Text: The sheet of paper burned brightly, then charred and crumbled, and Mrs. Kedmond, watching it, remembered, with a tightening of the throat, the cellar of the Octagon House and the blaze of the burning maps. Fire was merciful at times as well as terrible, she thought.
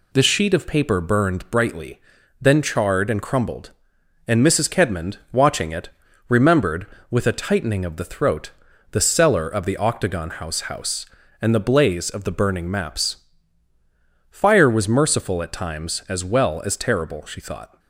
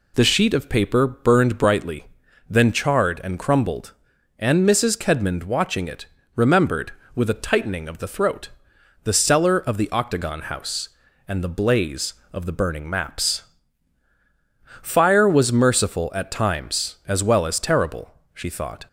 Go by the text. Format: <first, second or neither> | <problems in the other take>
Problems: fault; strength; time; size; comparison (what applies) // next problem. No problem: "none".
second | says "House" twice; at 10.6 s